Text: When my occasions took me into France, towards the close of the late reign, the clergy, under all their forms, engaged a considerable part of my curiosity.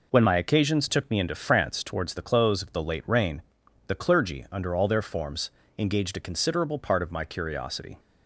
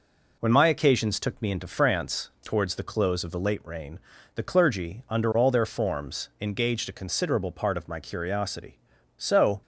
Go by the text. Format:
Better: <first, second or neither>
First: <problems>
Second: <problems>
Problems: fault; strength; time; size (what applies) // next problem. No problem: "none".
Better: first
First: none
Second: goes on to say "So"; slight; from 9.1 s on; 0.44 s long